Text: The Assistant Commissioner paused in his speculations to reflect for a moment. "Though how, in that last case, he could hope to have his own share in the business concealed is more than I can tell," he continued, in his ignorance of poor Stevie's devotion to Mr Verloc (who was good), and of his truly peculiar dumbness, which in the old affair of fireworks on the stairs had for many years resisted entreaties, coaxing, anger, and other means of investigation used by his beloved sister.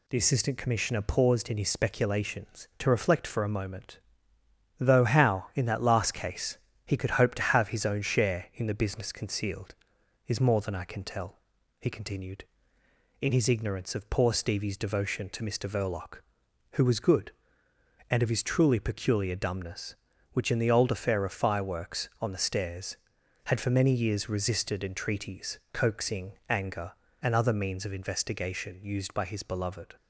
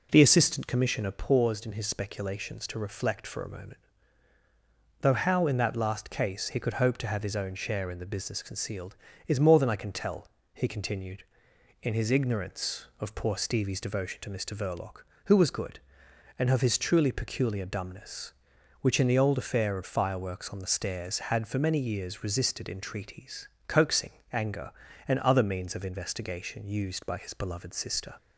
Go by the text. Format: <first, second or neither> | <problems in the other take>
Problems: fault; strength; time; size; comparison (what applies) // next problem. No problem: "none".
second | stops before "sister"; at 29.9 s